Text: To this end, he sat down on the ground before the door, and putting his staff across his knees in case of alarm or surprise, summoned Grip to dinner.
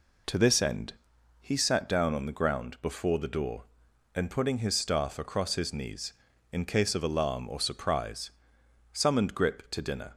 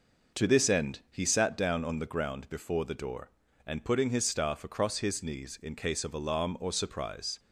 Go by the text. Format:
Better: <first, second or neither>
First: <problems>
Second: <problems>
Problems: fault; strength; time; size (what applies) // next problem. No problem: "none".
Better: first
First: none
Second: stops before "summoned Grip to dinner"; at 7.3 s